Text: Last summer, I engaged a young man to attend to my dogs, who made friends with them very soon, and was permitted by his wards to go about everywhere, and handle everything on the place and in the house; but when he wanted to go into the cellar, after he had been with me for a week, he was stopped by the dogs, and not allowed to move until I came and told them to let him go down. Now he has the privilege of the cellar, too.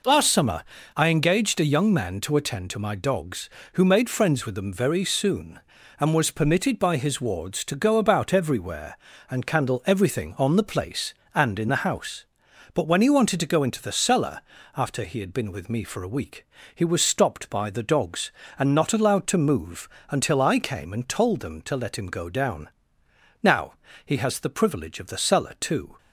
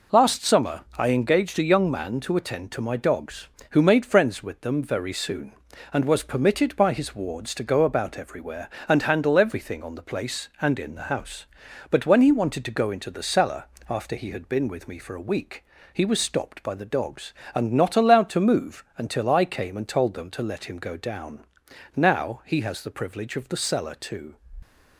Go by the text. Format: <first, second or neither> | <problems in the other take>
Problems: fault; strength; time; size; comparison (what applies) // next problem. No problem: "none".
second | says "candle" for "handle"; at 9.4 s // pauses between "move" and "until"; slight; at 19.8 s; 0.22 s long // pauses between "Now" and "he"; slight; at 23.7 s; 0.32 s long